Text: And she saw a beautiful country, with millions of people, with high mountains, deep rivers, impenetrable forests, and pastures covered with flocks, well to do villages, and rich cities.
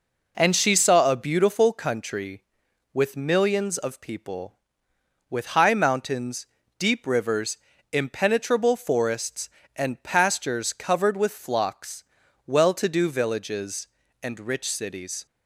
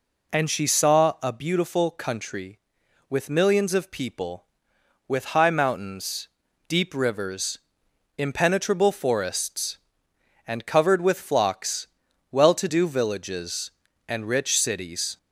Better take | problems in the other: first | skips "pastures"; at 10.6 s

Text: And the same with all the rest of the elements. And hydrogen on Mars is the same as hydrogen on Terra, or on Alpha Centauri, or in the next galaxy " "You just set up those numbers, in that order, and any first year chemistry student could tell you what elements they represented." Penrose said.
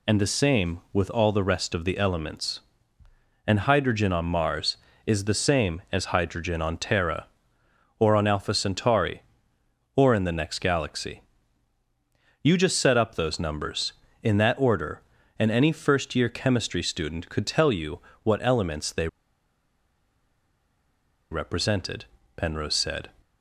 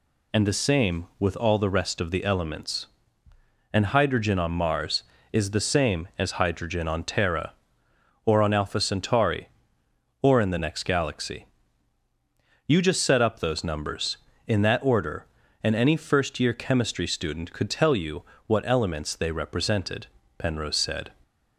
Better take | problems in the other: second | pauses between "you" and "what"; slight; at 17.9 s; 0.24 s long; slight in the second // pauses between "they" and "represented"; strong; at 19.0 s; 2.2 s long

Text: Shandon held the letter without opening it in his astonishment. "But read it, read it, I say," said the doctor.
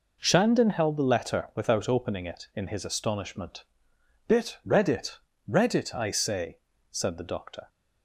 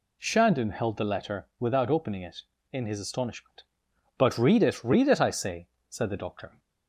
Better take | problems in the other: second | says "Bit" for "But"; at 4.2 s

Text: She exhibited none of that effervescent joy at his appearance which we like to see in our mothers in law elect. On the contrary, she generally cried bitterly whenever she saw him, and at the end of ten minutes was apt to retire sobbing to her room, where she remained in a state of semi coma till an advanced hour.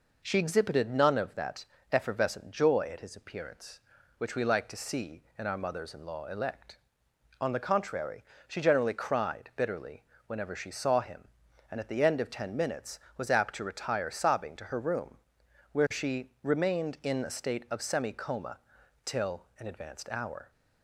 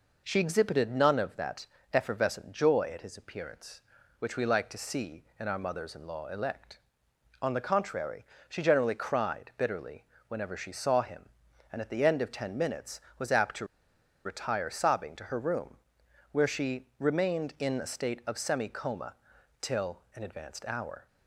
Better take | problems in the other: first | pauses between "that" and "effervescent"; slight; at 1.6 s; 0.26 s long; slight in the first // pauses between "bitterly" and "whenever"; slight; at 10.0 s; 0.24 s long; slight in the first // pauses between "to" and "retire"; noticeable; at 13.6 s; 0.58 s long // pauses between "coma" and "till"; noticeable; at 19.1 s; 0.46 s long; noticeable in the first

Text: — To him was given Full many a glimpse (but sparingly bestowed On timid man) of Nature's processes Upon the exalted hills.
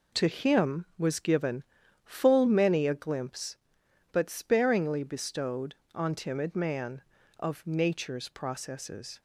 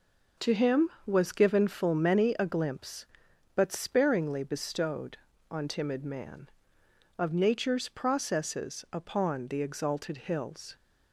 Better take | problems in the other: second | pauses between "given" and "Full"; at 1.6 s; 0.42 s long // stops before "Upon the exalted hills"; at 9.1 s

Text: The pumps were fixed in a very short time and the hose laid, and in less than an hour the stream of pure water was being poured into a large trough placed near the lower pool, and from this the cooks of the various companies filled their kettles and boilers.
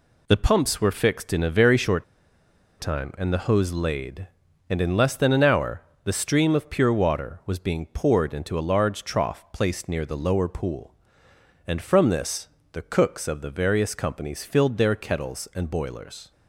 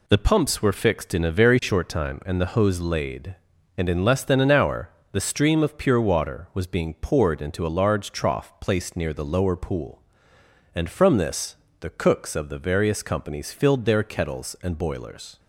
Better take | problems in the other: second | pauses between "short" and "time"; noticeable; at 2.0 s; 0.76 s long // pauses between "hour" and "the"; slight; at 5.8 s; 0.22 s long; slight in the second // pauses between "this" and "the"; slight; at 12.4 s; 0.24 s long; slight in the second

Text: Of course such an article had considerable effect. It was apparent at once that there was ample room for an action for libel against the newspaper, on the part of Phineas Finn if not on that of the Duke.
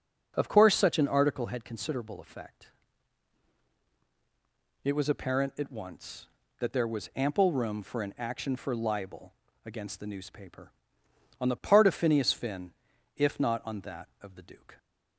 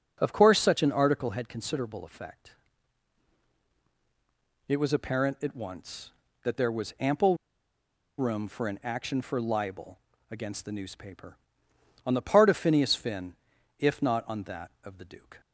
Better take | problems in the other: first | starts louder than the rest; until 1.2 s; 6.5 dB; also in the first // pauses between "ample" and "room"; noticeable; at 7.3 s; 0.81 s long // pauses between "libel" and "against"; slight; at 9.9 s; 0.32 s long; slight in the first // pauses between "Finn" and "if"; at 13.3 s; 0.44 s long; also in the first

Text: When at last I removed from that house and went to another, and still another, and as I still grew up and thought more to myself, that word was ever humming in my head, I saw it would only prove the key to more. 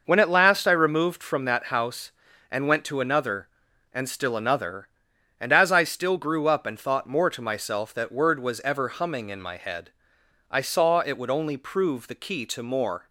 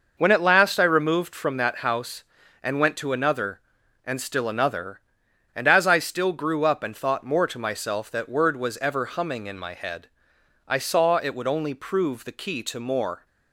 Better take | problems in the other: neither | none

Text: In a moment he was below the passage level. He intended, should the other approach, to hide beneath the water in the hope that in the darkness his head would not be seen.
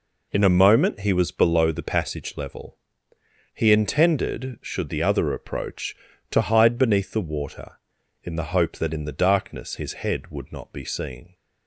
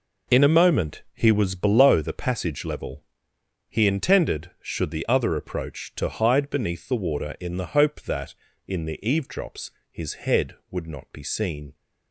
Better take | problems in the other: first | says "eavedrops" for "darkness"; at 9.0 s

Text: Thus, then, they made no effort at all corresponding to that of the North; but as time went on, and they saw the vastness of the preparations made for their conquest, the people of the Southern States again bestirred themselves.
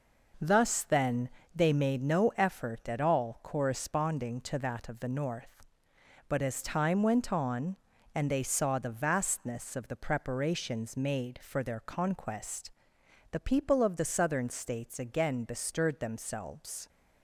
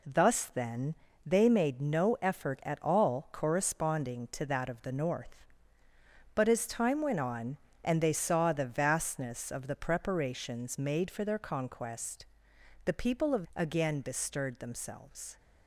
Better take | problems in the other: first | skips "the Southern States"; at 13.4 s

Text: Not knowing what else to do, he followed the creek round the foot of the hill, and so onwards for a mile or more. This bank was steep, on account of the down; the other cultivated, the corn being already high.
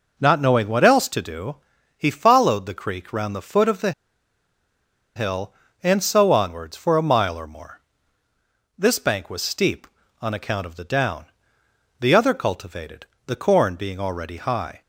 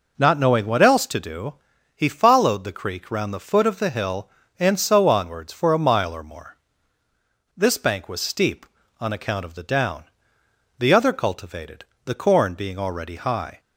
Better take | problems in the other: second | pauses between "the" and "hill"; strong; at 3.9 s; 1.2 s long

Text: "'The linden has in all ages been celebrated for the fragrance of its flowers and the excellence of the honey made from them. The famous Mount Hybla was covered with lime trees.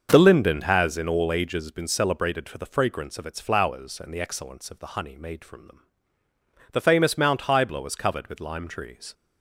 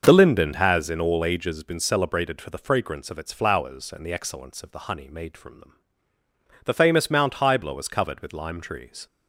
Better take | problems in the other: neither | starts louder than the rest; the same in both

